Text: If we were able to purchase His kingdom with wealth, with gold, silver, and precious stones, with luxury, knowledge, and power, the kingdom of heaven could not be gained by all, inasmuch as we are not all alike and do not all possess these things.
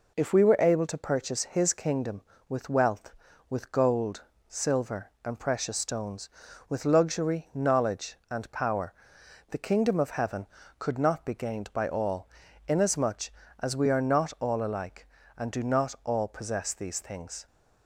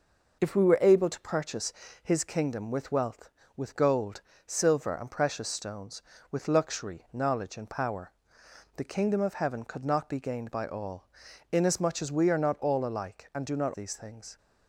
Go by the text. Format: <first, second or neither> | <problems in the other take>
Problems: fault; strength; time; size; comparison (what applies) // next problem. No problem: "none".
first | pauses between "purchase" and "His"; slight; at 1.7 s; 0.28 s long // skips "all possess"; at 13.7 s